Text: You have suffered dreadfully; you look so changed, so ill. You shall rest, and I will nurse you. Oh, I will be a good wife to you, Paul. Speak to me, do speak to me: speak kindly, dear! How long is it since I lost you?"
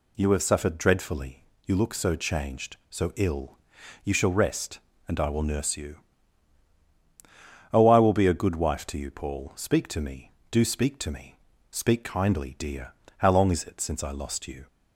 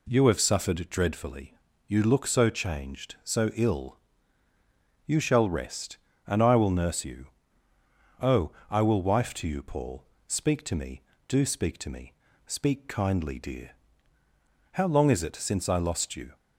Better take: first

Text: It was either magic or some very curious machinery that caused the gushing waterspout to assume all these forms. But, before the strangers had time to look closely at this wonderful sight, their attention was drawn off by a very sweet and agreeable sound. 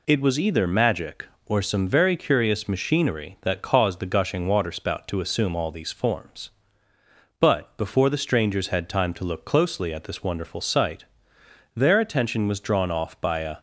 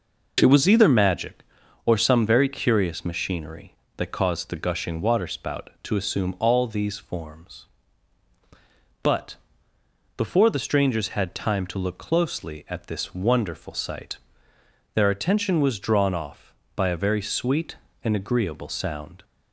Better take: second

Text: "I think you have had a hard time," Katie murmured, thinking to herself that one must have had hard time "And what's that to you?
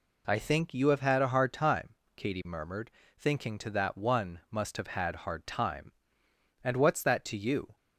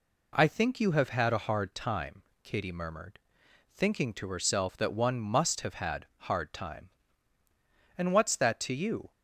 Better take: second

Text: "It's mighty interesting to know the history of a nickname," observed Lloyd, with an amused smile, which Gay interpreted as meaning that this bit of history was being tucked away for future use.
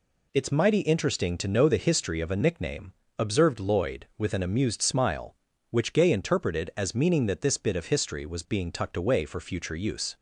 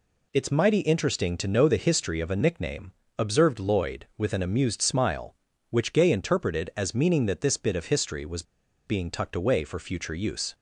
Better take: first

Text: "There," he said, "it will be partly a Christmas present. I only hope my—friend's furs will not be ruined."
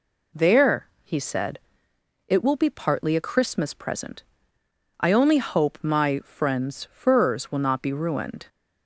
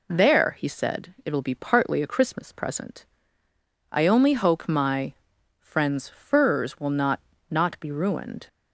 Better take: first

